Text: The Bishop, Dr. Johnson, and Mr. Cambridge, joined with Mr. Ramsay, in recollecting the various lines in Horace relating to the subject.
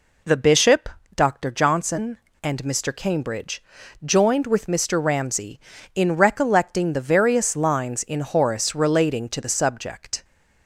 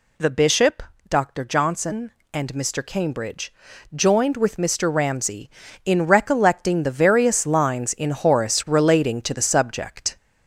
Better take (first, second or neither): first